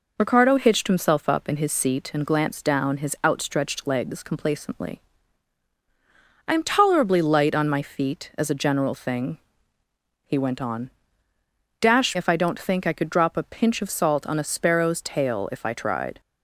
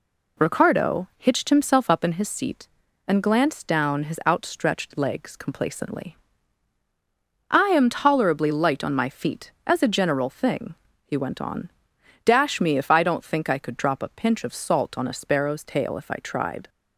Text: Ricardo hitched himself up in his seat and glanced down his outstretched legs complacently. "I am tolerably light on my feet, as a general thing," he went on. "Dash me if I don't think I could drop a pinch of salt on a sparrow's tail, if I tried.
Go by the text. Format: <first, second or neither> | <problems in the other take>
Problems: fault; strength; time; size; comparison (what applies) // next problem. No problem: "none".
second | skips "me"; at 12.1 s